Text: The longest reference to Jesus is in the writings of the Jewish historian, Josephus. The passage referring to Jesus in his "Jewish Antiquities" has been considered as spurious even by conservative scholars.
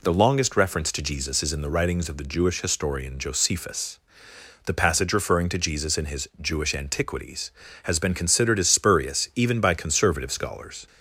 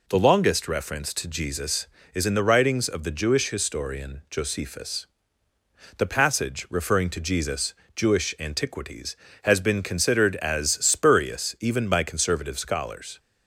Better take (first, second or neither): first